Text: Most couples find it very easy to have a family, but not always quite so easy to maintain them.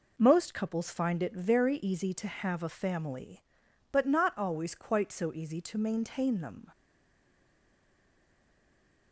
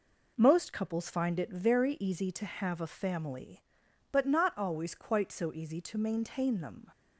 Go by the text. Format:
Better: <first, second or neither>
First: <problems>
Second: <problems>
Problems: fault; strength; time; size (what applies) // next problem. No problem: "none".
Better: second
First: stays silent after the last word; from 6.7 s on; 2.4 s long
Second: none